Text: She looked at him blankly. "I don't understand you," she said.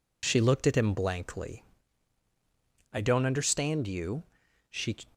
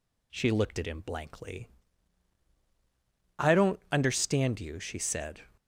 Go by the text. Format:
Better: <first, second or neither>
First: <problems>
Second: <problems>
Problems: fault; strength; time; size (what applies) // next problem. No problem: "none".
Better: second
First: stops before "said"; at 5.1 s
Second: none